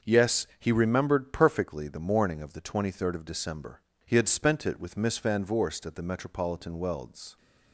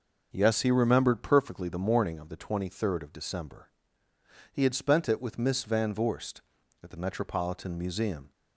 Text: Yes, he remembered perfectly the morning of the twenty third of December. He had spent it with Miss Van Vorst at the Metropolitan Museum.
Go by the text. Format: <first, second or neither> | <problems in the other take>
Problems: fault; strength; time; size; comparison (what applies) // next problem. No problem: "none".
second | starts louder than the rest; until 1.1 s; 6.5 dB // says "Welds" for "Museum"; at 6.7 s